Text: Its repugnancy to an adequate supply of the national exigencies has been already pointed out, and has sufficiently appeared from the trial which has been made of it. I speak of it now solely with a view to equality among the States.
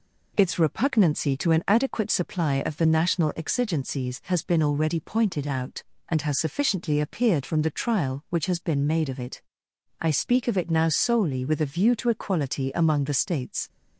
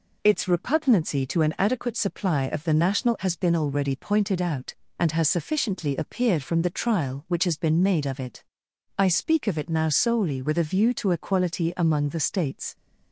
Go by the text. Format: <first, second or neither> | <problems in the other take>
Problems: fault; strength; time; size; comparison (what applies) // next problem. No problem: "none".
first | skips "exigencies"; at 3.1 s